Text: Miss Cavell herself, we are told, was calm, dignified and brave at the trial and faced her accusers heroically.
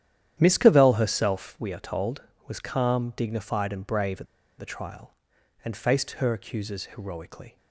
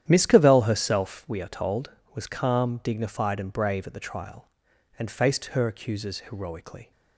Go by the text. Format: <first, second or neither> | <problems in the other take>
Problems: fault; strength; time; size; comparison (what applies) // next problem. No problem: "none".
second | starts louder than the rest; strong; until 1.4 s; 10.5 dB; strong in the second // pauses between "at" and "the"; slight; at 4.2 s; 0.34 s long